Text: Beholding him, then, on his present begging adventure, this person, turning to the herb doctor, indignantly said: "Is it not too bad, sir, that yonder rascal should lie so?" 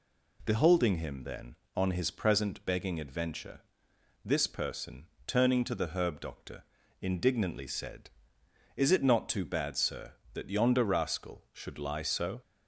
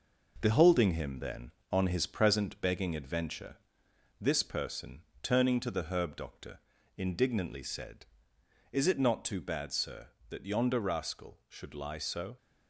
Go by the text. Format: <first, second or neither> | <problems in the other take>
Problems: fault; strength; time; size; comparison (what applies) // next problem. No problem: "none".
first | gets quieter; noticeable; throughout; 5 dB